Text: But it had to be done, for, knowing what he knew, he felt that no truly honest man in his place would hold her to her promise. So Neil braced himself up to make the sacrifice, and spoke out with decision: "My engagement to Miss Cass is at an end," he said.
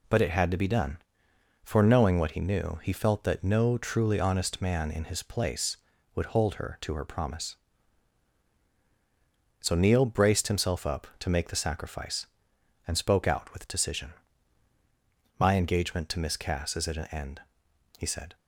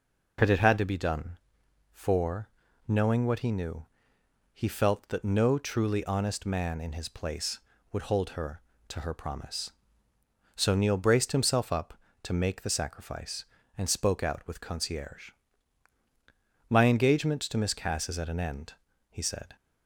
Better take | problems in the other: first | says "concierge" for "decision"; at 14.6 s

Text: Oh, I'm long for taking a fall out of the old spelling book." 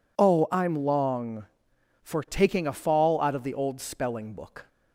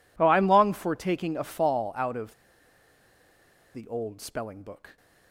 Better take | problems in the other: first | pauses between "of" and "the"; strong; at 2.3 s; 1.4 s long

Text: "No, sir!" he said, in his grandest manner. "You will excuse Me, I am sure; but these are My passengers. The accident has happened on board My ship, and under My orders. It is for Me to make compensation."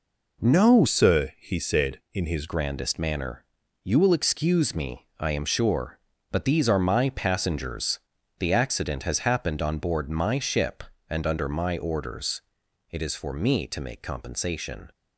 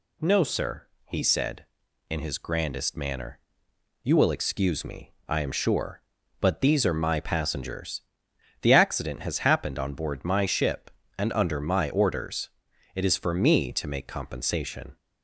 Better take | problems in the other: second | changes voice from "sir" to "his"; from 0.8 to 2.4 s; 1.6 s long

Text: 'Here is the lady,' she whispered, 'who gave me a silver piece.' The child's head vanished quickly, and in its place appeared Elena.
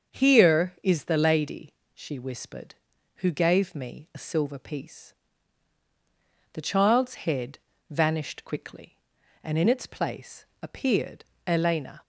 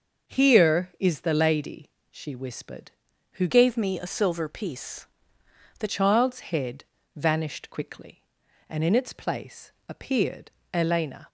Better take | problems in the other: first | starts louder than the rest; until 1.3 s; 6 dB; also in the first // changes voice from "gave" to "The"; from 3.4 to 5.8 s; 2.4 s long // pauses between "head" and "vanished"; slight; at 6.8 s; 0.32 s long; slight in the first // pauses between "place" and "appeared"; slight; at 9.7 s; 0.16 s long; slight in the first // pauses between "appeared" and "Elena"; slight; at 10.5 s; 0.22 s long; slight in the first

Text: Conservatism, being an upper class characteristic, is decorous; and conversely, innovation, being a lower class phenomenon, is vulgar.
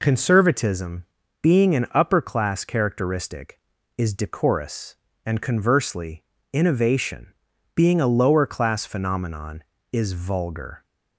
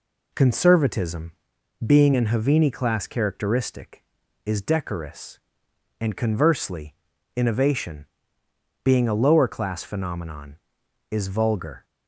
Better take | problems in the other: first | says "havini" for "upper"; at 2.2 s

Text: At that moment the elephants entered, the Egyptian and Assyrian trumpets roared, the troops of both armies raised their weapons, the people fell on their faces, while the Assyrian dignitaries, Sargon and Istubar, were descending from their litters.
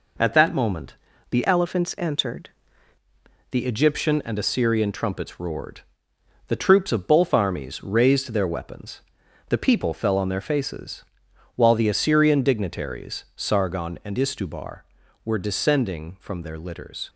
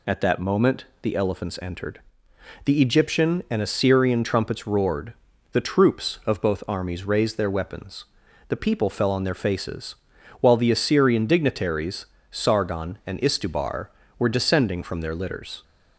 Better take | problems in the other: second | pauses between "moment" and "the"; slight; at 0.9 s; 0.34 s long; slight in the second // changes voice from "elephants" to "entered"; from 1.4 to 2.4 s; 1.0 s long

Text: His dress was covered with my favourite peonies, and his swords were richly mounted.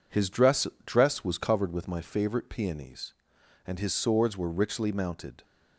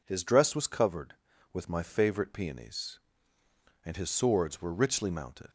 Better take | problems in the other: second | says "dress" twice; at 0.8 s

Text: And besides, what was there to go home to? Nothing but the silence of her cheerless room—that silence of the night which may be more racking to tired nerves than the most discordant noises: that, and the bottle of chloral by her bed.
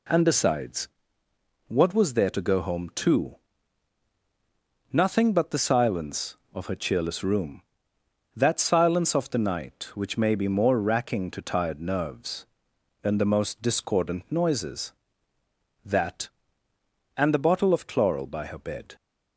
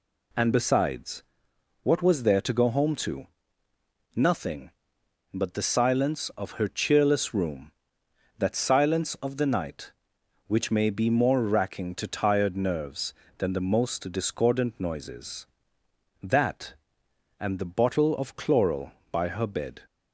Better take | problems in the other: neither | none

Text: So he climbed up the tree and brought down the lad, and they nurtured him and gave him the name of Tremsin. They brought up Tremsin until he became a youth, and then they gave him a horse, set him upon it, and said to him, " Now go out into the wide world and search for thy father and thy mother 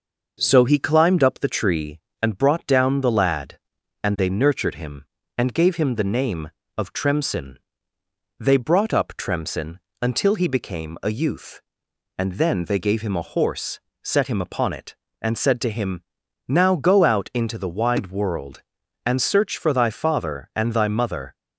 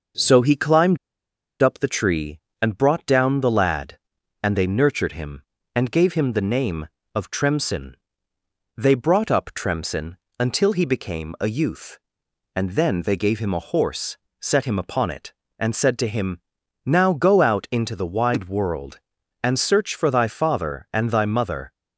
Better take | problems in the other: first | pauses between "climbed" and "up"; noticeable; at 0.9 s; 0.62 s long // pauses between "Tremsin" and "until"; slight; at 10.1 s; 0.22 s long; slight in the first

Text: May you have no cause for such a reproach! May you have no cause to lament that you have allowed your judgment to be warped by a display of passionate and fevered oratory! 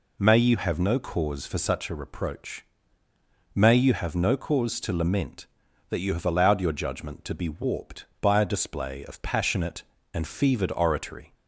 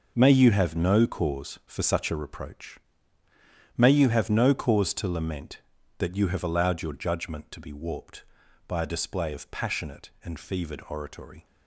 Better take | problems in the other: first | gets quieter; strong; throughout; 10.5 dB

